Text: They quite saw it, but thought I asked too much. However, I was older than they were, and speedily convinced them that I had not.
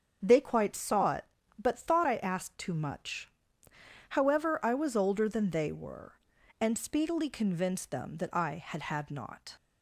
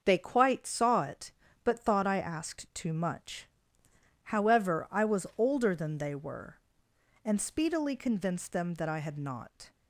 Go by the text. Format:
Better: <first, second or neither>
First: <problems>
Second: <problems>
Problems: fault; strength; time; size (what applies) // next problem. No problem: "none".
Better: second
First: starts louder than the rest; until 1.2 s; 7 dB // says "had" twice; at 8.8 s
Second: starts louder than the rest; until 1.0 s; 6.5 dB